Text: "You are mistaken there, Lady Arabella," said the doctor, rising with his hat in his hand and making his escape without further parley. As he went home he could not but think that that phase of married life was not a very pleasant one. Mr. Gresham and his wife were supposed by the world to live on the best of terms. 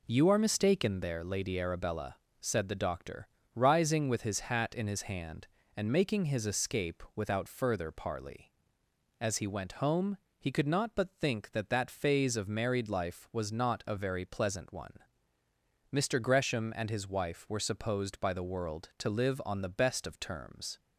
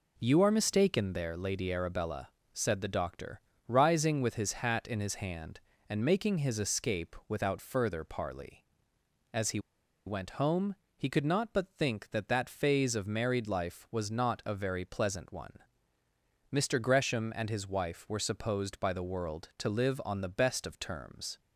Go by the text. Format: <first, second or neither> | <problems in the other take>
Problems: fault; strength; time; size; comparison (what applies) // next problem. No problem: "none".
first | pauses between "he" and "went"; noticeable; at 9.5 s; 0.47 s long // pauses between "home" and "he"; slight; at 10.7 s; 0.20 s long; slight in the first